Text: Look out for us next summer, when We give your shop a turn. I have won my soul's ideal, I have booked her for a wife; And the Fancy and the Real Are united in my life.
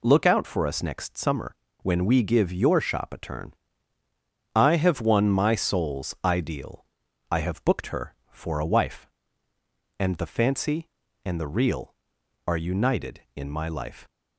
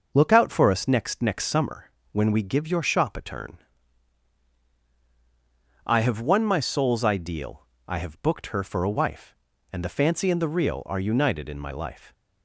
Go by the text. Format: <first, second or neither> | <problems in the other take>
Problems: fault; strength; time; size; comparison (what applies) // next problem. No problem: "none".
first | says "next" twice; at 1.2 s